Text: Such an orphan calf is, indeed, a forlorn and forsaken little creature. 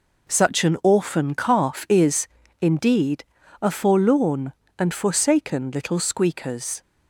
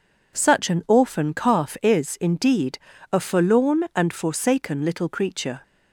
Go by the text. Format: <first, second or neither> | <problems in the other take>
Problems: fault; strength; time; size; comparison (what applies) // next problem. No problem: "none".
second | says "squeakers" for "creature"; at 5.9 s